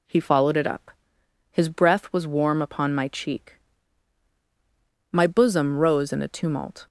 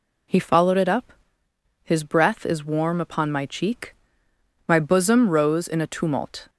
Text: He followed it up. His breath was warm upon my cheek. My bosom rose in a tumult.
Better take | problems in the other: first | says "is" for "was"; at 2.4 s

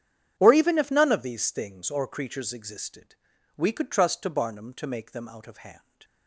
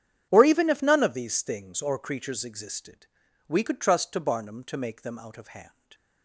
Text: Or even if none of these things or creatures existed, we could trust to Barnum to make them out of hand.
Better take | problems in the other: neither | starts louder than the rest; strong; the same in both

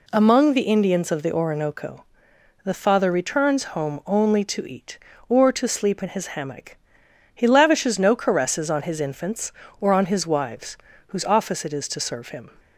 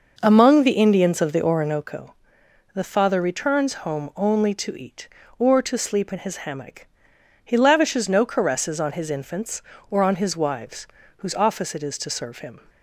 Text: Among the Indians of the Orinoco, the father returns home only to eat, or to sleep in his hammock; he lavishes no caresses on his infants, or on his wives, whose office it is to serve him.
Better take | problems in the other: first | starts louder than the rest; noticeable; until 1.8 s; 5.5 dB

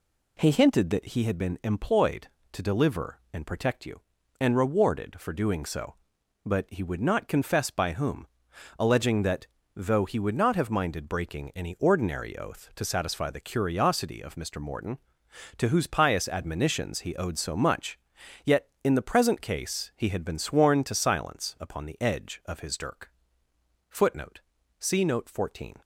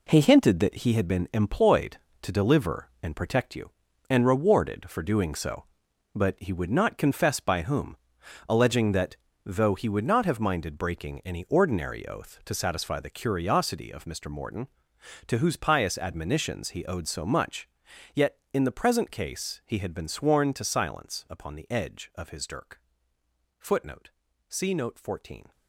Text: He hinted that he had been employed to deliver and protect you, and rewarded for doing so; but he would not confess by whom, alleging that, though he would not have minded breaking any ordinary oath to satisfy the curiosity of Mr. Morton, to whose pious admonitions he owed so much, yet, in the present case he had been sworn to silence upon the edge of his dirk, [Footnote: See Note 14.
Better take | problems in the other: first | gets quieter; strong; throughout; 9 dB

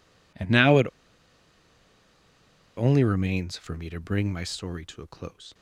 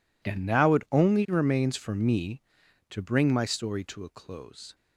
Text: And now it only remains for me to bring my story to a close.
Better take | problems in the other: second | pauses between "it" and "only"; strong; at 0.8 s; 1.9 s long

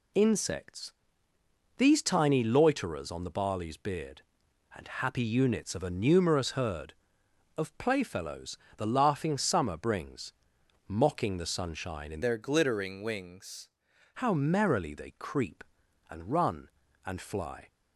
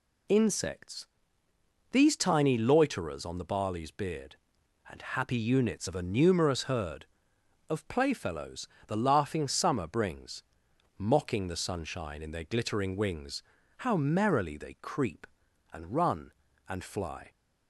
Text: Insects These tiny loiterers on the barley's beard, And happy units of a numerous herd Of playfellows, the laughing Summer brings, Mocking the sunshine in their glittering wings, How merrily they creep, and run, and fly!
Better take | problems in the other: second | pauses between "Insects" and "These"; noticeable; at 0.9 s; 0.86 s long; noticeable in the second // changes voice from "their" to "wings"; from 12.2 to 13.6 s; 1.4 s long

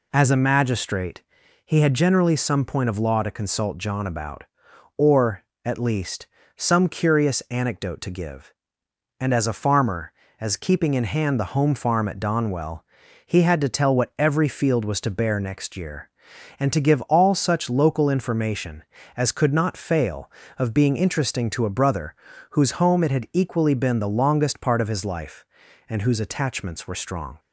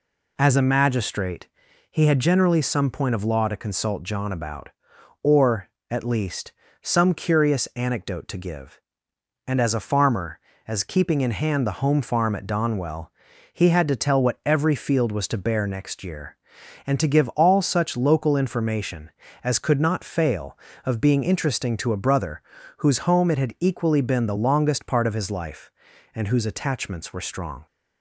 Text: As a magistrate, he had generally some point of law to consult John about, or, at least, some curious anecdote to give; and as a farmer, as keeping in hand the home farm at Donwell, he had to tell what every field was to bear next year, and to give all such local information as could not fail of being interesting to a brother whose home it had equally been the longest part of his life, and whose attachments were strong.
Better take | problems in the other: neither | pauses between "brother" and "whose"; the same in both

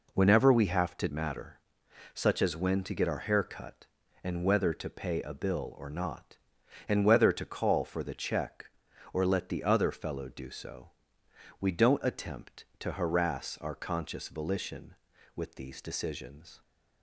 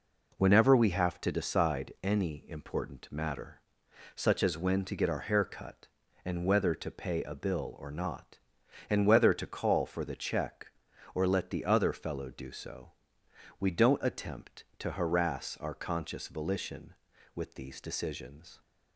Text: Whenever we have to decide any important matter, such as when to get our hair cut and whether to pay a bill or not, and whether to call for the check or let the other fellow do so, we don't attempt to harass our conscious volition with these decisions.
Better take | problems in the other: second | skips "decide any important"; at 1.0 s

